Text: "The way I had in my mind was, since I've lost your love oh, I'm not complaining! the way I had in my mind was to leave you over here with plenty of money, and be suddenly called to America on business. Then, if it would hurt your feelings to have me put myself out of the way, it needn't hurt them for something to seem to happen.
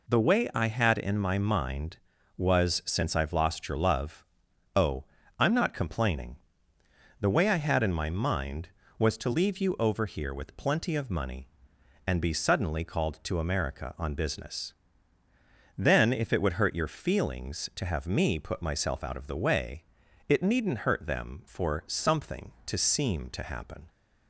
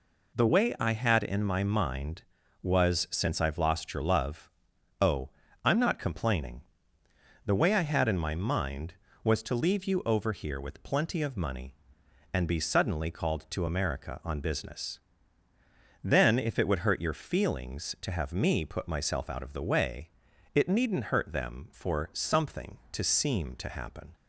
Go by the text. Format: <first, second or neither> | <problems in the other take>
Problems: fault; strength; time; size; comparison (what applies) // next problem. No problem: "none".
neither | pauses between "love" and "oh"; noticeable; the same in both